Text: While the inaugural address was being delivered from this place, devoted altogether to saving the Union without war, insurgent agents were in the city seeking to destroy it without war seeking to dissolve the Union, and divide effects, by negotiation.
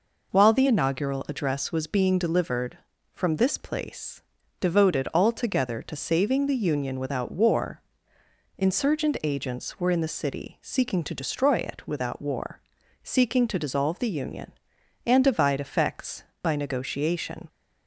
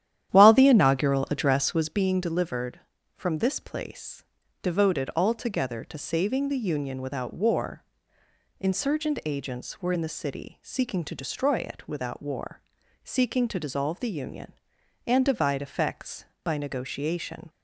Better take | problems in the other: first | starts louder than the rest; strong; until 2.0 s; 11 dB // pauses between "war" and "seeking"; at 12.6 s; 0.40 s long; also in the first

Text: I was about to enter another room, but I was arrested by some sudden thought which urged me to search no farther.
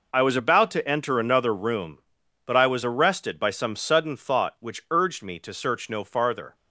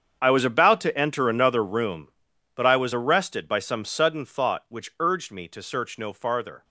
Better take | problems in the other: first | gets quieter; strong; throughout; 16 dB

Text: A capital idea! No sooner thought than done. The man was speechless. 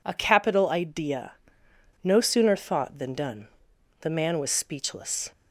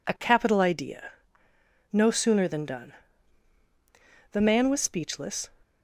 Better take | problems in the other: first | skips "thought"; at 2.4 s

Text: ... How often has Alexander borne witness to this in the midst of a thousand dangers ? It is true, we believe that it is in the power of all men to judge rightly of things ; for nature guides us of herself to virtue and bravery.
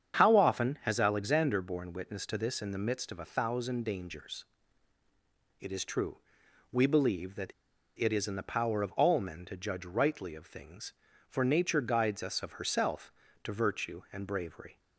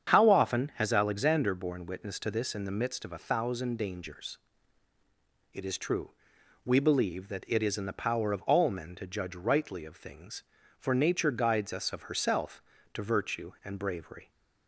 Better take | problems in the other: second | starts louder than the rest; strong; until 1.2 s; 8 dB; strong in the second // pauses between "that" and "it"; at 7.5 s; 0.45 s long

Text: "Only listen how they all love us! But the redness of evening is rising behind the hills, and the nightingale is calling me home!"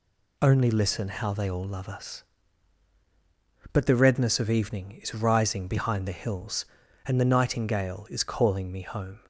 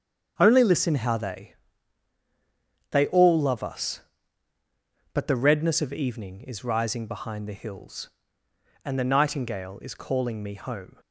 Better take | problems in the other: first | starts louder than the rest; strong; until 1.3 s; 7.5 dB // says "they" twice; at 2.8 s

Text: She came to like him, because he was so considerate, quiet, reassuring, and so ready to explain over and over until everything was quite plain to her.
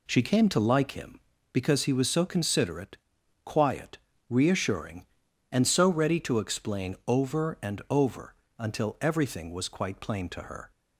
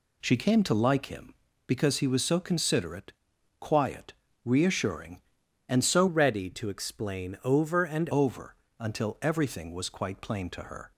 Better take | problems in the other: first | changes voice from "ready" to "and"; from 6.0 to 8.0 s; 2.0 s long // pauses between "over" and "until"; slight; at 8.5 s; 0.24 s long; slight in the first

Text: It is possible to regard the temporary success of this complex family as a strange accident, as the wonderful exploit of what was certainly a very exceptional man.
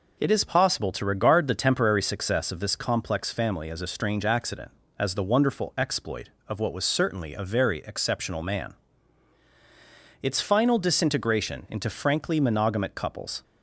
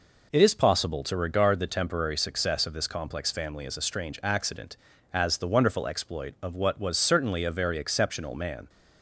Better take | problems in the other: second | goes on to say "Its final disintegration into frankly monogamic couples"; strong; from 10.2 s on; 3.2 s long

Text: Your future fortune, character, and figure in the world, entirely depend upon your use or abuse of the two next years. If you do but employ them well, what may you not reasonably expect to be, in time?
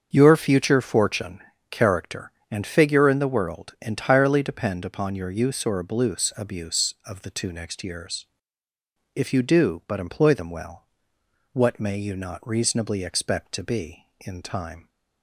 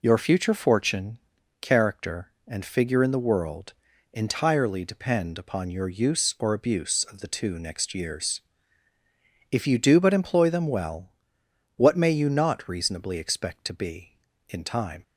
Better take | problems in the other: second | starts louder than the rest; until 1.1 s; 7 dB // says "abuse" twice; at 6.3 s

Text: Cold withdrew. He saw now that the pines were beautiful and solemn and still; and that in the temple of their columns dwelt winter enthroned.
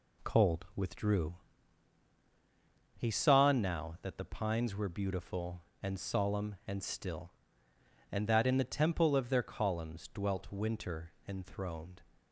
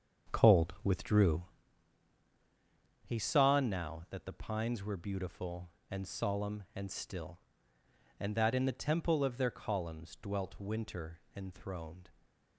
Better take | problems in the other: first | starts louder than the rest; until 1.7 s; 7 dB

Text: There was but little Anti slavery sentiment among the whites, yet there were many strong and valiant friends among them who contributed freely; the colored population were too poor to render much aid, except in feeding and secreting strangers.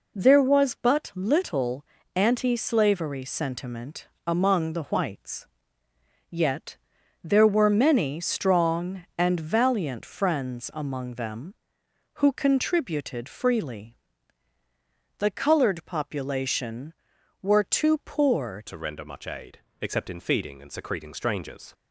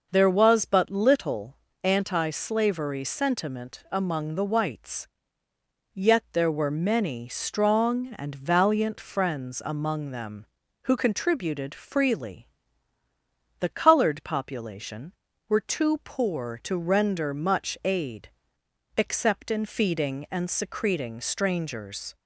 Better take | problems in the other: second | pauses between "little" and "Anti"; slight; at 1.8 s; 0.32 s long; slight in the second // pauses between "sentiment" and "among"; slight; at 4.0 s; 0.22 s long // pauses between "yet" and "there"; noticeable; at 6.7 s; 0.46 s long // changes voice at "to"; from 18.6 s on; 3.1 s long

